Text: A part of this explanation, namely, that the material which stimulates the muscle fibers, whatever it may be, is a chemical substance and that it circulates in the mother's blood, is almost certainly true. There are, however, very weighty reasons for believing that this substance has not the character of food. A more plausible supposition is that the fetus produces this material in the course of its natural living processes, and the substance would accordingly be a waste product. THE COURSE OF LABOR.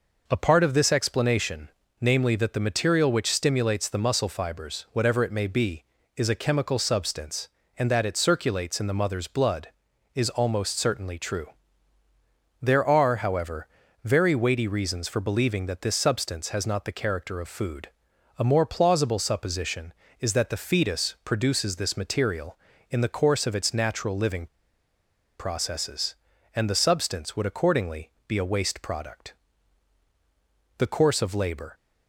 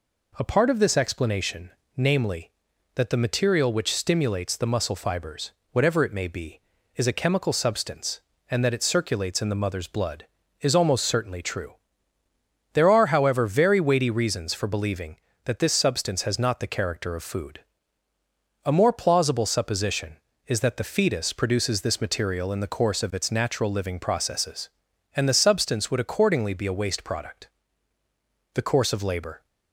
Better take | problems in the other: second | pauses between "living" and "processes"; noticeable; at 24.4 s; 0.91 s long // pauses between "accordingly" and "be"; slight; at 28.1 s; 0.18 s long

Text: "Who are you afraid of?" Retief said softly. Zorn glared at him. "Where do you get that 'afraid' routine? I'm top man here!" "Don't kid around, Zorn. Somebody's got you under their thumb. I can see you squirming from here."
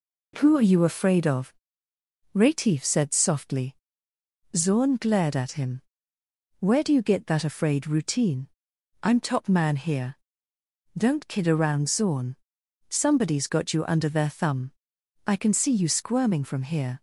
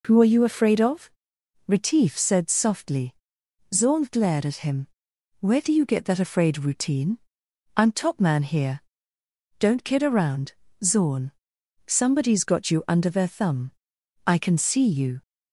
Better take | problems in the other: first | stops before "squirming from here"; at 15.2 s

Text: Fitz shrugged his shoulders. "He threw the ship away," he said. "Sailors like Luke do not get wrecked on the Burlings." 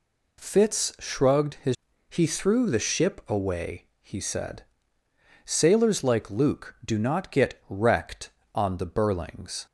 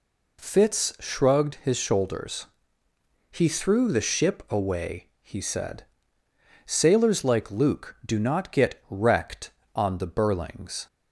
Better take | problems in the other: second | skips "shoulders"; at 1.9 s

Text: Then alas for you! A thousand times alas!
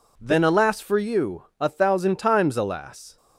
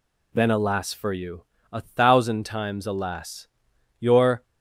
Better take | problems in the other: first | goes on to say "Your"; slight; from 3.9 s on; 0.44 s long

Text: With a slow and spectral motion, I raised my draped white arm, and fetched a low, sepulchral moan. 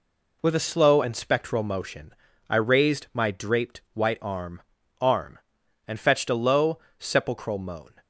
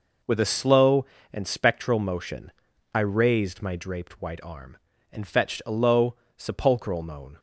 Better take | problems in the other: second | says "arm" twice; at 5.0 s

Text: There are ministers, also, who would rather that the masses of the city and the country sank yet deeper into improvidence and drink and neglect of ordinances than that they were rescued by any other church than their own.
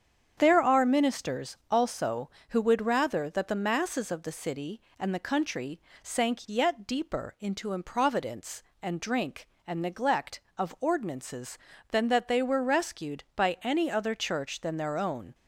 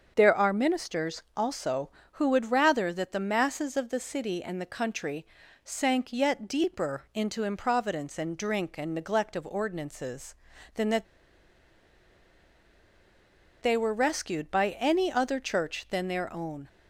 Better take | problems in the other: first | starts louder than the rest; until 1.1 s; 7 dB; strong in the first // pauses between "country" and "sank"; at 5.2 s; 0.40 s long; slight in the first // pauses between "that" and "they"; strong; at 11.0 s; 2.5 s long

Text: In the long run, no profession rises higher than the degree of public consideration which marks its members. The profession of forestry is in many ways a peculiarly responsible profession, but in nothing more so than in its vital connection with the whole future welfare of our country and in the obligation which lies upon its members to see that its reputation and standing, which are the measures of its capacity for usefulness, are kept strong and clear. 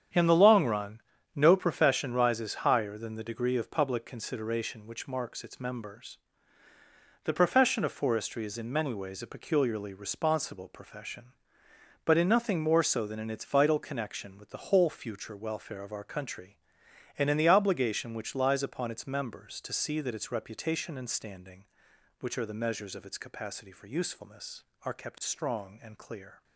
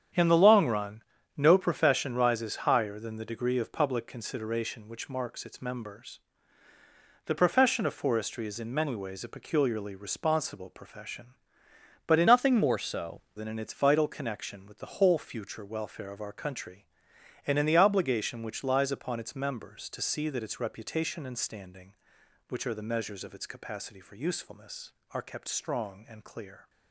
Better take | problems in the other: first | starts louder than the rest; strong; until 1.5 s; 8.5 dB; strong in the first // changes voice from "nothing" to "so"; from 12.2 to 13.2 s; 1.0 s long

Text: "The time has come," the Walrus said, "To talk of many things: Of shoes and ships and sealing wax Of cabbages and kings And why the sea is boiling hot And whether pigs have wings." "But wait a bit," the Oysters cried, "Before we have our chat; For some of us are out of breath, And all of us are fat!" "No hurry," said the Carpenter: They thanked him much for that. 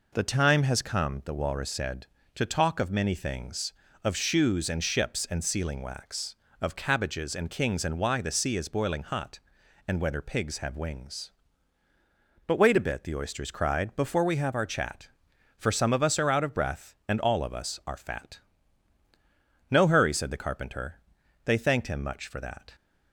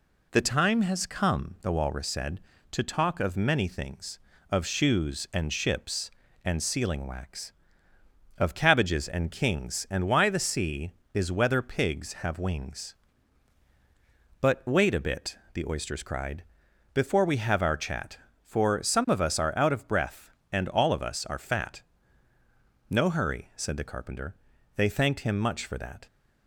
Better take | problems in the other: first | skips "boiling hot And"; at 11.3 s

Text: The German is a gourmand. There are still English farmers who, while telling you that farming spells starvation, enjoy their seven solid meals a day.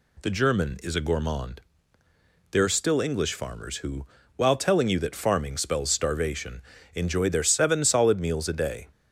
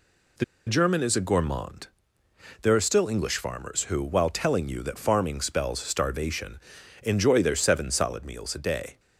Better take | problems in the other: first | pauses between "The" and "German"; slight; at 0.4 s; 0.22 s long

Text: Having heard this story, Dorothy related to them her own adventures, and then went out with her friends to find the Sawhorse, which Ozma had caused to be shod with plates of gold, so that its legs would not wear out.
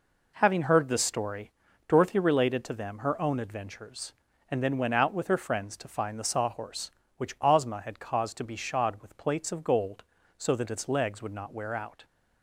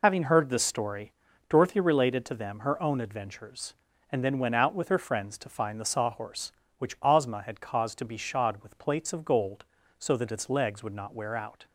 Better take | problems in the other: first | loses the start of "Having"; at 0.0 s; 70 ms

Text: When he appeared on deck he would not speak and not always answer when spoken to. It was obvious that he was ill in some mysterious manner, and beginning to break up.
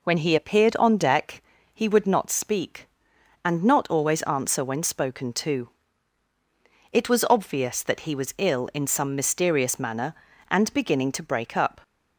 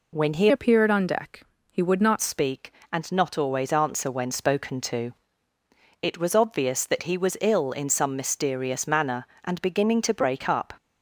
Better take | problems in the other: first | changes voice from "appeared" to "not"; from 0.5 to 2.2 s; 1.7 s long // pauses between "deck" and "he"; slight; at 1.4 s; 0.28 s long; slight in the first

